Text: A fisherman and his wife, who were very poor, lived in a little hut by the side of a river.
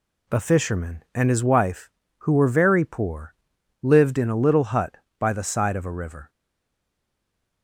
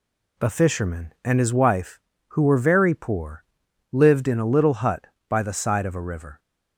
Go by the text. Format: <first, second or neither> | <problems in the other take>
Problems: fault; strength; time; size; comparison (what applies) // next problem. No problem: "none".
second | stays silent after the last word; noticeable; from 6.2 s on; 1.4 s long